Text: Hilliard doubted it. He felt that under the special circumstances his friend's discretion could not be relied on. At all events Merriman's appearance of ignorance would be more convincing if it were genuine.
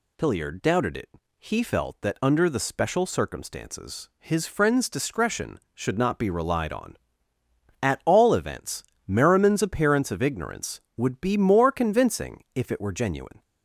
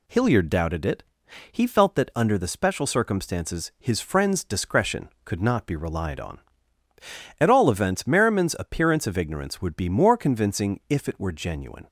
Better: second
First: says "should" for "could"; at 5.7 s // pauses between "events" and "Merriman's"; slight; at 8.8 s; 0.22 s long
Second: none

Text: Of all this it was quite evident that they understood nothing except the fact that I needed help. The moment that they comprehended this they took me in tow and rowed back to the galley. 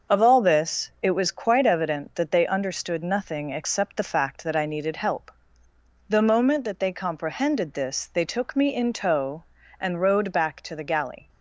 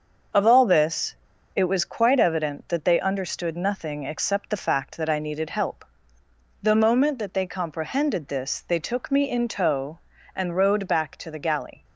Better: first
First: starts louder than the rest; until 1.2 s; 6.5 dB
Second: starts louder than the rest; until 1.7 s; 6.5 dB // pauses between "this" and "it"; at 1.1 s; 0.41 s long

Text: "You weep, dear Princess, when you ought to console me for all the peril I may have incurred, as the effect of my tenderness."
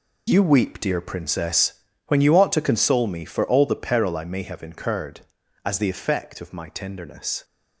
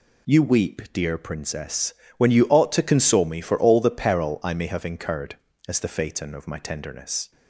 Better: first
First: none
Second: says "phaeton" for "effect"; at 5.8 s

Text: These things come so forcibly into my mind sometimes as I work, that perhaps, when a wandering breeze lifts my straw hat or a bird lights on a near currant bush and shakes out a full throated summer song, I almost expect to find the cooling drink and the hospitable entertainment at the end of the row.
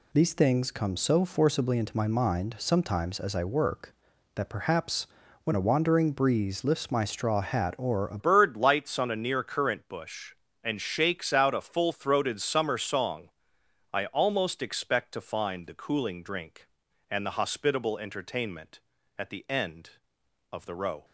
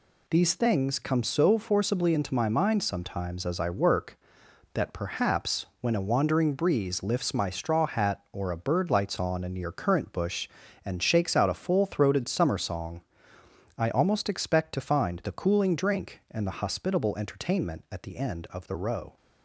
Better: second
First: changes voice at "bird"; from 8.1 s on; 12.9 s long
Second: none

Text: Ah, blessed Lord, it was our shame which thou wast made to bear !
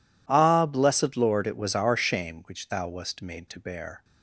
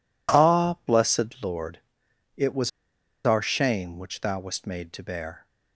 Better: first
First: none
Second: pauses between "was" and "our"; noticeable; at 2.6 s; 0.55 s long

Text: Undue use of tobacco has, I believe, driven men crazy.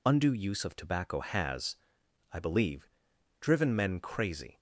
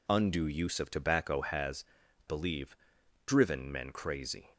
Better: first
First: none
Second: skips "I"; at 2.0 s

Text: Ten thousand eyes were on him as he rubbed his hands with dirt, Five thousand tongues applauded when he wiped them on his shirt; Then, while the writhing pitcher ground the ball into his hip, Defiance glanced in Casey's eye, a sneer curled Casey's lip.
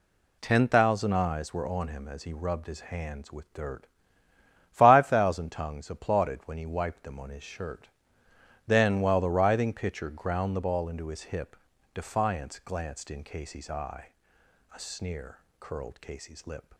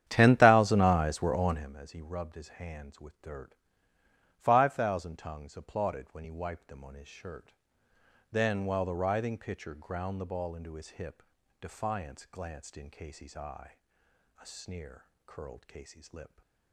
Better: first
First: pauses between "sneer" and "curled"; slight; at 15.3 s; 0.22 s long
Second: starts louder than the rest; strong; until 1.7 s; 10.5 dB // pauses between "sneer" and "curled"; slight; at 15.0 s; 0.22 s long

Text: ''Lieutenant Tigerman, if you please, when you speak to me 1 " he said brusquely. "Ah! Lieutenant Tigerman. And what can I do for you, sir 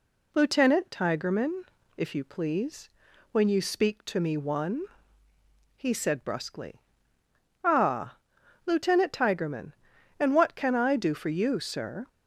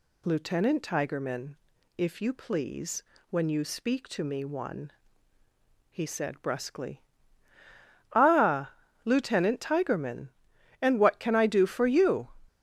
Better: first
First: none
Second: stops before "sir"; at 12.4 s

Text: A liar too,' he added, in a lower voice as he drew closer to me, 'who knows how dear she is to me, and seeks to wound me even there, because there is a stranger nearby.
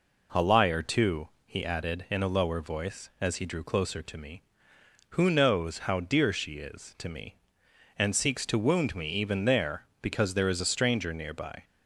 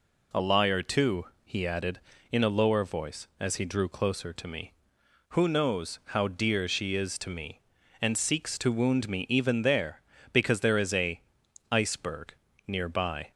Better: first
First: none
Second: says "iceberg" for "stranger"; at 11.7 s

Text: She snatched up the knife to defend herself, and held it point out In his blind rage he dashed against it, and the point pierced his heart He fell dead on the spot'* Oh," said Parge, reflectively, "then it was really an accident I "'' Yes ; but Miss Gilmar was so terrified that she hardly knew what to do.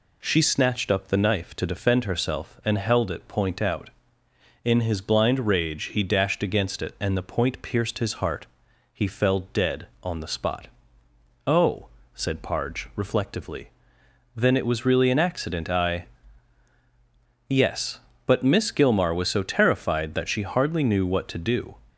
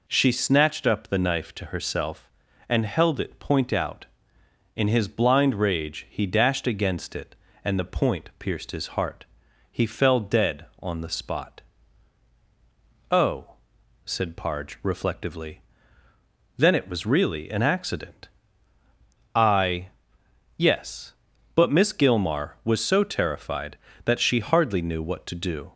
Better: first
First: pauses between "heart" and "He"; noticeable; at 8.4 s; 0.48 s long // pauses between "spot" and "Oh"; noticeable; at 10.6 s; 0.80 s long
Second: skips "defend"; at 1.6 s // pauses between "heart" and "He"; at 9.2 s; 0.44 s long // pauses between "spot" and "Oh"; strong; at 11.5 s; 1.5 s long // pauses between "accident" and "I"; at 18.2 s; 1.0 s long

